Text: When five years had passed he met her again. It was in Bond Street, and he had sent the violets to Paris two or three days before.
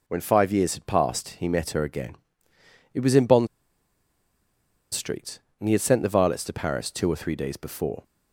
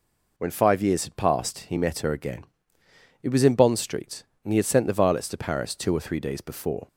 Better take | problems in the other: second | pauses between "Bond" and "Street"; strong; at 3.4 s; 1.4 s long

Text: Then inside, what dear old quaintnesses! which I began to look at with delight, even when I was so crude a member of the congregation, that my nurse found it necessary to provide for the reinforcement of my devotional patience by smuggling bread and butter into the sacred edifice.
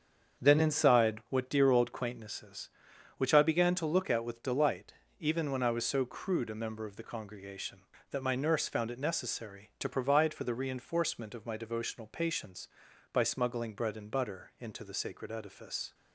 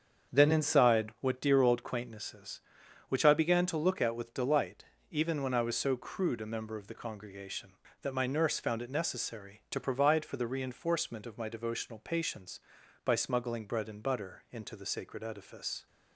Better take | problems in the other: neither | starts louder than the rest; strong; the same in both

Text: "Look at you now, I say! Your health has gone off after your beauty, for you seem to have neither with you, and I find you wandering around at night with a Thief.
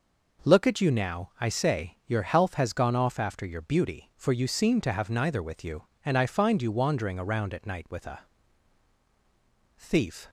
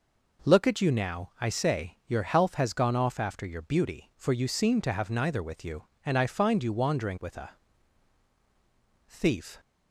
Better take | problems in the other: first | skips "around at night"; at 7.1 s // pauses between "a" and "Thief"; strong; at 7.5 s; 1.5 s long; strong in the first

